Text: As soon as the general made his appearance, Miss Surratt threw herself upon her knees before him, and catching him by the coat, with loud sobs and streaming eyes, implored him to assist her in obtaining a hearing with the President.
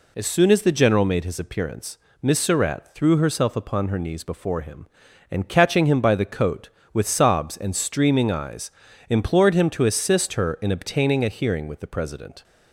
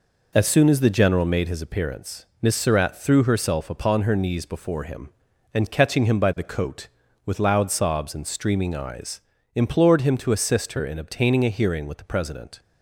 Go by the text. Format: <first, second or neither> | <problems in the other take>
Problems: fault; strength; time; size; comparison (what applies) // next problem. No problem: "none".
second | skips "loud"; at 7.0 s